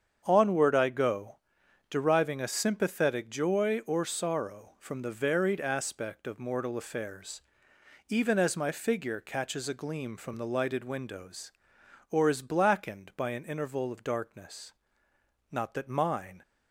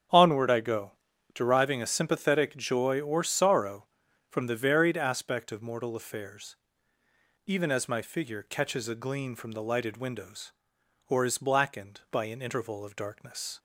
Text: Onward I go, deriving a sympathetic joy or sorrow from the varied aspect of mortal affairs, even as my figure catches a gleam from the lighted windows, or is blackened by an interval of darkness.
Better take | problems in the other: second | starts louder than the rest; strong; until 1.2 s; 7.5 dB; strong in the second // goes on to say "Not that mine"; noticeable; from 15.5 s on; 0.90 s long

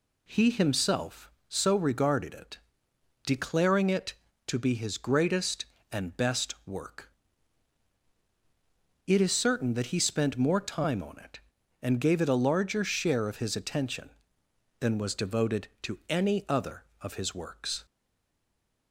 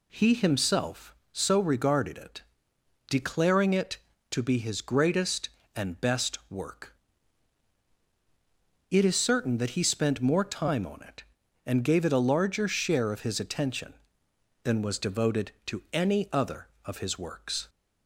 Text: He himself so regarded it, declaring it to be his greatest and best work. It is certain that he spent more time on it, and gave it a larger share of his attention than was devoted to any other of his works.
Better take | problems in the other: second | stays silent after the last word; from 17.8 s on; 1.1 s long

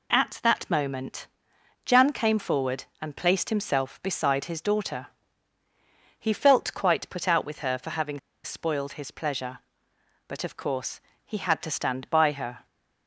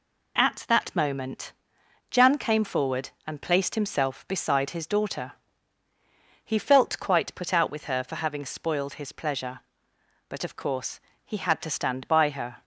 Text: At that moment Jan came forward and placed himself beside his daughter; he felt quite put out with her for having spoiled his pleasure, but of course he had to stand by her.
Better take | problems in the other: second | pauses between "moment" and "Jan"; noticeable; at 1.2 s; 0.58 s long; noticeable in the second // pauses between "having" and "spoiled"; slight; at 8.1 s; 0.24 s long // pauses between "course" and "he"; slight; at 10.9 s; 0.24 s long; slight in the second

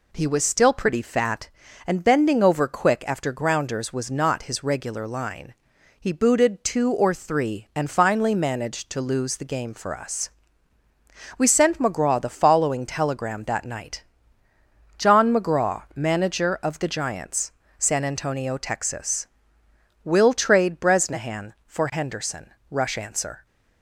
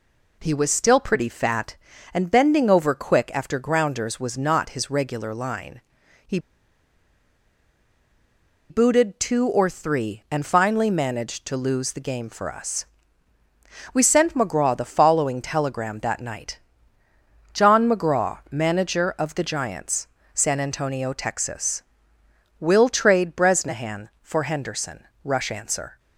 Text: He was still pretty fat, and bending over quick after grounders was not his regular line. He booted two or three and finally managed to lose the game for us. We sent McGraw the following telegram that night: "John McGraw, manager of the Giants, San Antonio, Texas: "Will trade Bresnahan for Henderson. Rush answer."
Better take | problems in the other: first | pauses between "He" and "booted"; strong; at 6.3 s; 2.3 s long

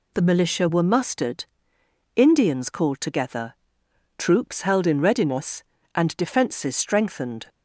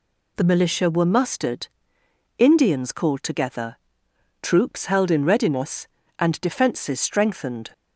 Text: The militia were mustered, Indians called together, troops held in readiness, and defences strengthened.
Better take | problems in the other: neither | none

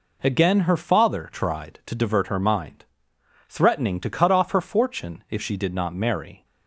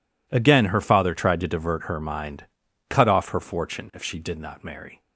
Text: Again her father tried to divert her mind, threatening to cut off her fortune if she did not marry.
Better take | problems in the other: first | skips "threatening to"; at 2.6 s

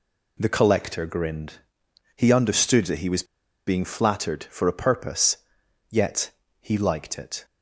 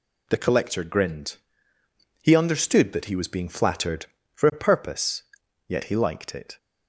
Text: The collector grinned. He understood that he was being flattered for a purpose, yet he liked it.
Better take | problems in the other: second | pauses between "was" and "being"; at 3.2 s; 0.42 s long // pauses between "yet" and "he"; slight; at 6.3 s; 0.30 s long

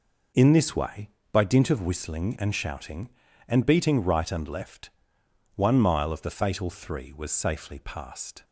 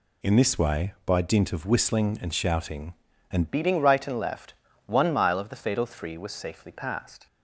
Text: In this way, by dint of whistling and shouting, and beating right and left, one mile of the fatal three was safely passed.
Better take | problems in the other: first | changes voice at "beating"; from 3.5 s on; 3.7 s long

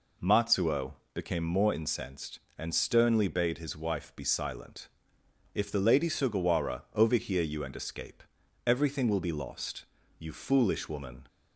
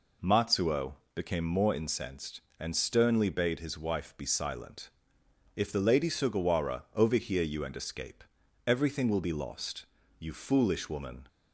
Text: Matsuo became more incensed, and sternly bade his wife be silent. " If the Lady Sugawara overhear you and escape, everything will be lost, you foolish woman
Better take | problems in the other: neither | pauses between "Matsuo" and "became"; slight; the same in both

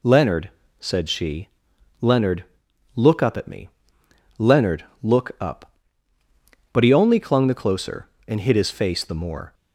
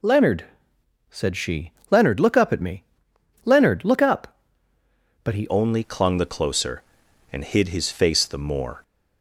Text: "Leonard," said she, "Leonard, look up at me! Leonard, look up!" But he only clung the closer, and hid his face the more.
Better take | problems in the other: first | changes voice at "only"; from 5.4 s on; 3.4 s long

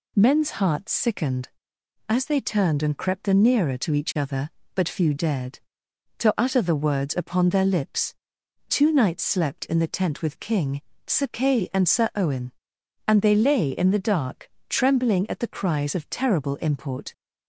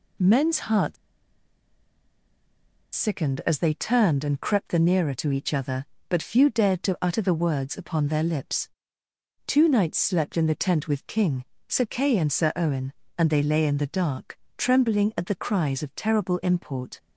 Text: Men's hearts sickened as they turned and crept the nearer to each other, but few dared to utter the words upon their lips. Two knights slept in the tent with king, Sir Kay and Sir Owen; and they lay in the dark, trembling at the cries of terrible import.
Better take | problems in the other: first | pauses between "hearts" and "sickened"; strong; at 0.9 s; 1.9 s long

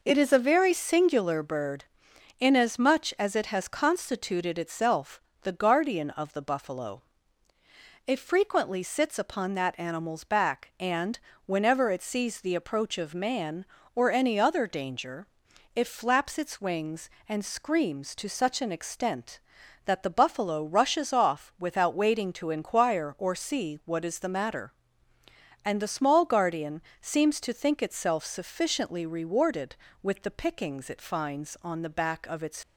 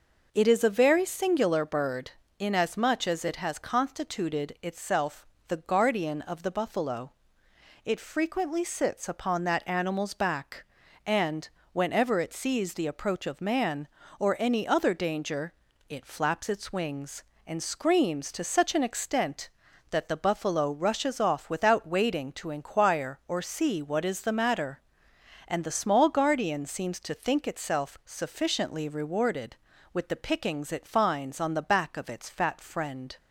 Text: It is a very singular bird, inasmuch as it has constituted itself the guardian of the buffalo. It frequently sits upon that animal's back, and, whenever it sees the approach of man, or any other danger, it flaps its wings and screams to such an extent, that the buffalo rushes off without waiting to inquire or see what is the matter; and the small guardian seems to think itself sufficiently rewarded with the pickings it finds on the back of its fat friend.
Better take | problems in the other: second | pauses between "itself" and "the"; slight; at 5.2 s; 0.20 s long; slight in the second // pauses between "guardian" and "seems"; slight; at 26.8 s; 0.18 s long // stops before "fat friend"; at 32.6 s

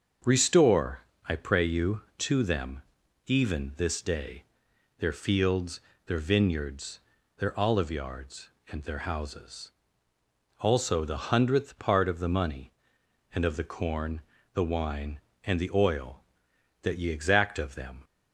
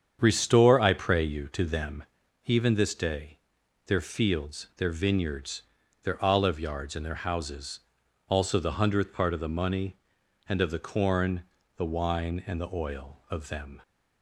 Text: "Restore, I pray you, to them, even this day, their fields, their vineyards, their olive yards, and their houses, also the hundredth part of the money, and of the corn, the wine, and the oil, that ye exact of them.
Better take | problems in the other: first | starts louder than the rest; strong; until 1.2 s; 8 dB; also in the first // skips "that ye exact"; at 13.2 s

